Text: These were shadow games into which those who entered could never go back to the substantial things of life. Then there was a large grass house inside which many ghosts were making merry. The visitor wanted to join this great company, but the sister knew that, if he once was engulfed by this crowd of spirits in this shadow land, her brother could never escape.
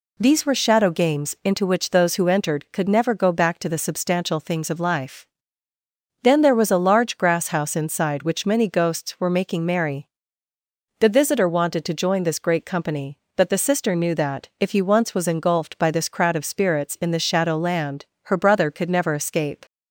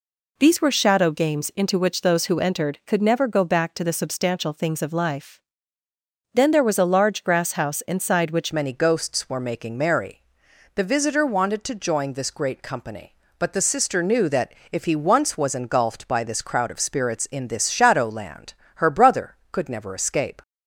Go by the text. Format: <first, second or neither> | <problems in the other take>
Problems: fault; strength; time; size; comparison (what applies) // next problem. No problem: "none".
first | changes voice at "many"; from 8.5 s on; 11.9 s long